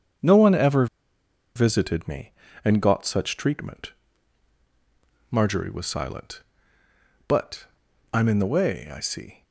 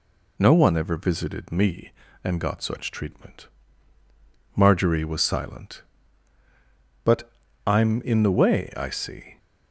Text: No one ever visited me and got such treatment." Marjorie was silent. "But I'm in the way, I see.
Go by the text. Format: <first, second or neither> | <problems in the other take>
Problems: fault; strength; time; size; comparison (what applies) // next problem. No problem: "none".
second | starts louder than the rest; strong; until 1.9 s; 7.5 dB // pauses between "ever" and "visited"; noticeable; at 0.8 s; 0.70 s long // pauses between "But" and "I'm"; noticeable; at 7.6 s; 0.48 s long; slight in the second